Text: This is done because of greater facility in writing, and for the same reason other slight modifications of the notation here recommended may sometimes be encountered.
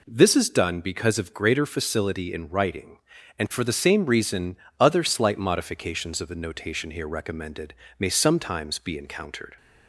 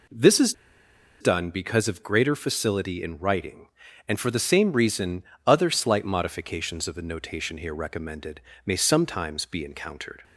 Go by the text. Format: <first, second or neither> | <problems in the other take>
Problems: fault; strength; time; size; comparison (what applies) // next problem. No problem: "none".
first | pauses between "is" and "done"; noticeable; at 0.5 s; 0.66 s long // pauses between "reason" and "other"; slight; at 5.2 s; 0.22 s long; slight in the first // pauses between "recommended" and "may"; slight; at 8.4 s; 0.24 s long; slight in the first